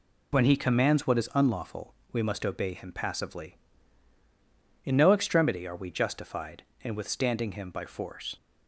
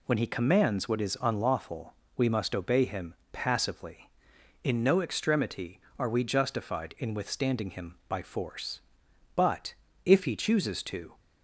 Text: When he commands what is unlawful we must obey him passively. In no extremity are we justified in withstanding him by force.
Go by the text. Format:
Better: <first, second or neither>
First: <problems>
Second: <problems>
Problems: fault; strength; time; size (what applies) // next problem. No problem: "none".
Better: first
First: pauses between "unlawful" and "we"; slight; at 1.9 s; 0.18 s long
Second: pauses between "unlawful" and "we"; slight; at 1.9 s; 0.22 s long // pauses between "him" and "passively"; slight; at 3.1 s; 0.18 s long // goes on to say "But if he chooses to"; strong; from 9.3 s on; 1.8 s long